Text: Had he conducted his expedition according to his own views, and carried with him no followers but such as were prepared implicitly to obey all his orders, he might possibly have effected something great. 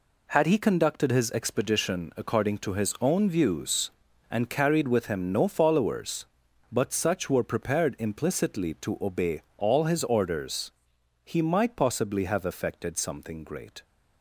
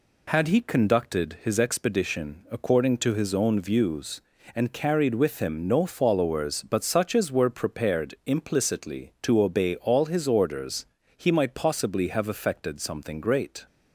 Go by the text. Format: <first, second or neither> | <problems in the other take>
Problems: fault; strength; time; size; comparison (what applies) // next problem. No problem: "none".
second | skips "as"; at 7.2 s // pauses between "obey" and "all"; slight; at 9.4 s; 0.16 s long